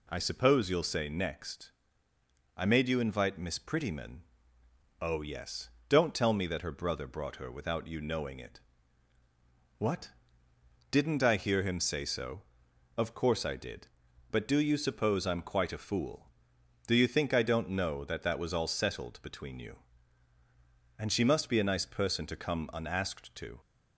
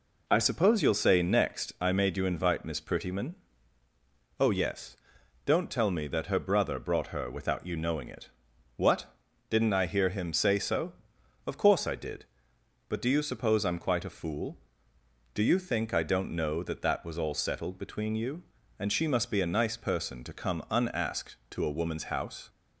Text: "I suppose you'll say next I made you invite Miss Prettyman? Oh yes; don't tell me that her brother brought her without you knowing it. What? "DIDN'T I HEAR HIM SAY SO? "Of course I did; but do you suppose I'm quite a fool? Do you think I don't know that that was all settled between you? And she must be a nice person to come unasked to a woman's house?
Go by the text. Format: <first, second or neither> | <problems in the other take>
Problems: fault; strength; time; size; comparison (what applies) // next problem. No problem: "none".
second | pauses between "next" and "I"; noticeable; at 1.7 s; 0.86 s long // stops before "a woman's house"; at 23.6 s